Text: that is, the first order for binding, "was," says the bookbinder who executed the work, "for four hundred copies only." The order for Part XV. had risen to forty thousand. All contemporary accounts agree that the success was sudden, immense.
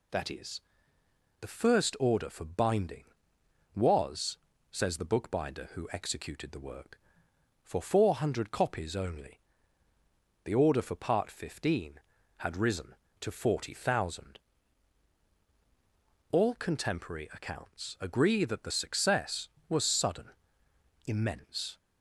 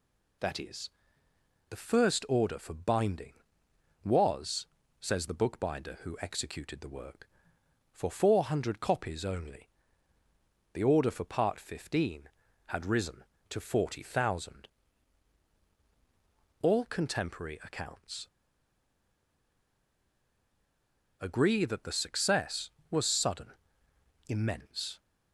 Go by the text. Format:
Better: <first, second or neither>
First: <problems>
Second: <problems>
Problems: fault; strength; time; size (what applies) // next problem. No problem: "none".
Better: first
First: none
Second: pauses between "accounts" and "agree"; strong; at 18.2 s; 2.9 s long